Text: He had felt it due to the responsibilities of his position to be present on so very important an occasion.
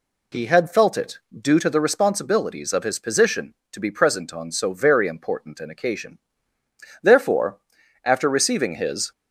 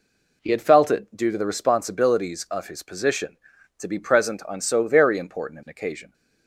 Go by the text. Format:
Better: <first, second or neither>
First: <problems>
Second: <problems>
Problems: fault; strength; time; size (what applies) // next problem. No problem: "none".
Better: second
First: pauses between "it" and "due"; slight; at 1.1 s; 0.20 s long // goes on to say "Therefore after receiving his"; strong; from 7.0 s on; 2.0 s long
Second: none